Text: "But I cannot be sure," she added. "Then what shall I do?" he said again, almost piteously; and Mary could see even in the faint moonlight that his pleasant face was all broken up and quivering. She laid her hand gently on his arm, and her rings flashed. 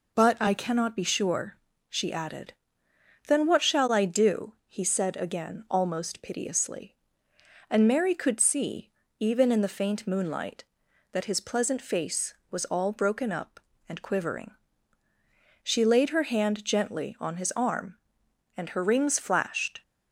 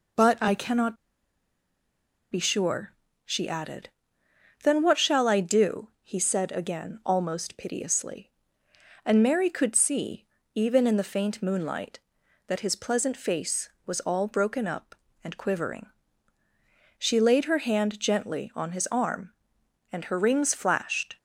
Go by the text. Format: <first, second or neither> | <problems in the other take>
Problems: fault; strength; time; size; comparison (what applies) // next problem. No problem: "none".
first | pauses between "cannot" and "be"; strong; at 0.9 s; 1.3 s long // pauses between "see" and "even"; slight; at 10.2 s; 0.26 s long; slight in the first